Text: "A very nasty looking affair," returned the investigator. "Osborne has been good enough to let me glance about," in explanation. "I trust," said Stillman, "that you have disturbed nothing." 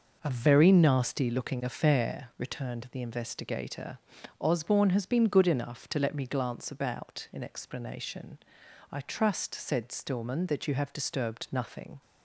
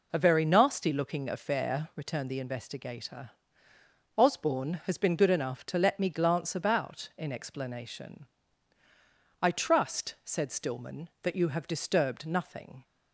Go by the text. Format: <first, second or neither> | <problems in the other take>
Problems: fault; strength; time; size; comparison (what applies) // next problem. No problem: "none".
neither | none